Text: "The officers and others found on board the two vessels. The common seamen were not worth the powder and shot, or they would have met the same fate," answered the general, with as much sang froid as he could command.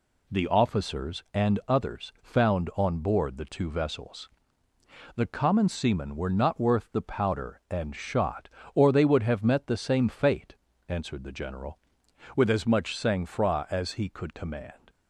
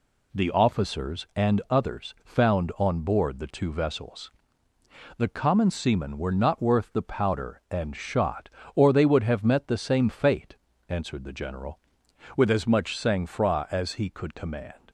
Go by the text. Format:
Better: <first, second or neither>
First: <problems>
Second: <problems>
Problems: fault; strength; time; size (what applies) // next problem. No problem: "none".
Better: neither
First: none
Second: none